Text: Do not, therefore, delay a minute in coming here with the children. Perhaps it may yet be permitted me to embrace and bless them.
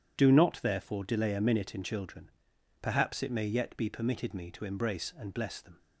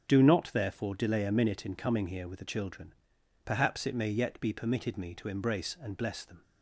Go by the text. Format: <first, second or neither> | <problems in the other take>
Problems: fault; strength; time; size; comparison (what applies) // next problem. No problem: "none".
second | starts louder than the rest; strong; until 1.2 s; 9 dB; strong in the second // skips "coming here with the"; at 1.8 s